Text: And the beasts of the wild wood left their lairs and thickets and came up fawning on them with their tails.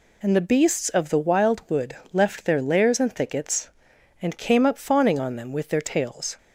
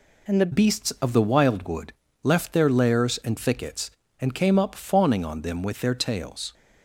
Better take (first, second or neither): first